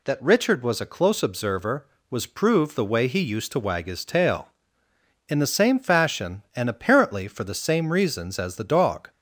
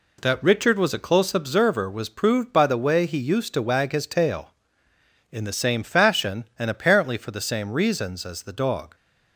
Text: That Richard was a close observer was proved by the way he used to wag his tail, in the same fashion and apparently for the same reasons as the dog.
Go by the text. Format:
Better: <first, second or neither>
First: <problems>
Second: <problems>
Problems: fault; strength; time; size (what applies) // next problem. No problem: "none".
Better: second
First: skips "by"; at 2.7 s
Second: none